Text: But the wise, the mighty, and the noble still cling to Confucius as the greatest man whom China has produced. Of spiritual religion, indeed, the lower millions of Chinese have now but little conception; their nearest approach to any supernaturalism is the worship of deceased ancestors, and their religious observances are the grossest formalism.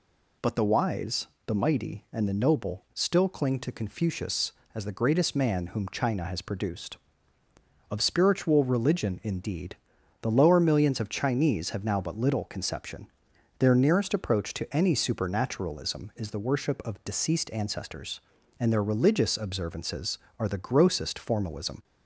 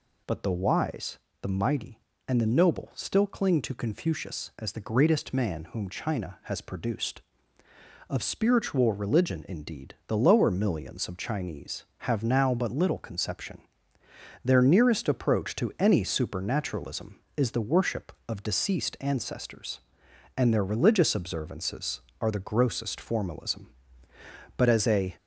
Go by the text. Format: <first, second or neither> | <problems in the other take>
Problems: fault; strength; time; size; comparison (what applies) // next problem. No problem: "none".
first | goes on to say "But as a"; from 24.5 s on; 0.60 s long